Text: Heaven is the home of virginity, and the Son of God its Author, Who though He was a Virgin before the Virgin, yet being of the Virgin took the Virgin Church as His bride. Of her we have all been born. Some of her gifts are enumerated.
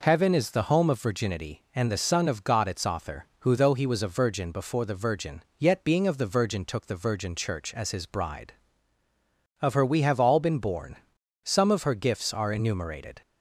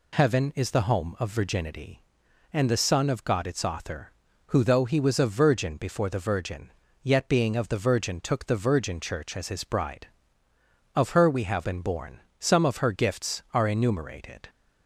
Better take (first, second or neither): first